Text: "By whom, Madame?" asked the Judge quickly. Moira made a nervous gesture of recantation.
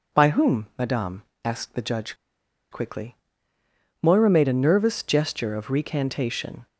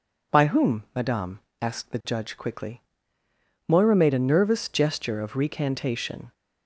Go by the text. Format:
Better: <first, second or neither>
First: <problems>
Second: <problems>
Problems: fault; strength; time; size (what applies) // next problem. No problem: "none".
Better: second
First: pauses between "Judge" and "quickly"; noticeable; at 2.1 s; 0.56 s long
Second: none